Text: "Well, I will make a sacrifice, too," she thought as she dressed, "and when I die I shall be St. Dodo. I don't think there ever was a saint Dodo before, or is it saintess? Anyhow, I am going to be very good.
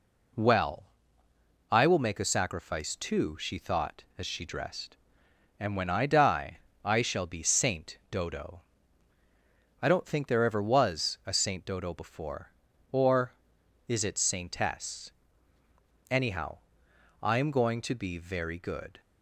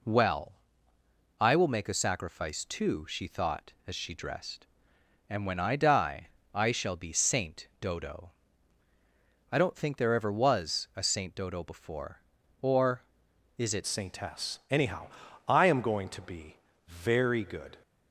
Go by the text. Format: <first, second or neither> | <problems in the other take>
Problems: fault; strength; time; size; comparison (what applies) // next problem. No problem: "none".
first | pauses between "die" and "I"; slight; at 6.2 s; 0.22 s long; slight in the first // changes voice at "saintess"; from 13.8 s on; 3.9 s long // pauses between "be" and "very"; slight; at 16.5 s; 0.28 s long